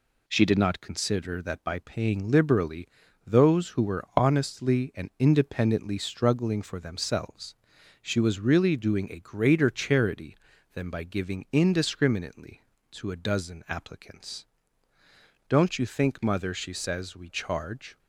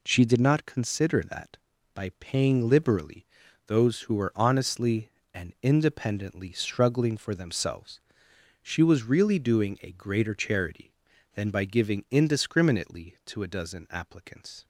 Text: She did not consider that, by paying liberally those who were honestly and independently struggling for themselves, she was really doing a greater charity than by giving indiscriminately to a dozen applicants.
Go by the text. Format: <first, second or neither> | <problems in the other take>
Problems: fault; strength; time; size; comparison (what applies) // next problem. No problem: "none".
second | pauses between "liberally" and "those"; at 2.8 s; 0.38 s long; also in the second // goes on to say "Don't you think mother she says we charge"; strong; from 15.5 s on; 2.4 s long